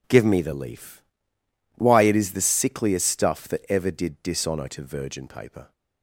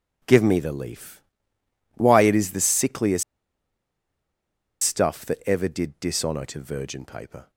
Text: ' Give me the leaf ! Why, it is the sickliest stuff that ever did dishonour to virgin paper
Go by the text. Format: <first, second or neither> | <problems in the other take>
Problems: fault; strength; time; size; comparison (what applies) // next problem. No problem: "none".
first | pauses between "sickliest" and "stuff"; strong; at 3.2 s; 1.6 s long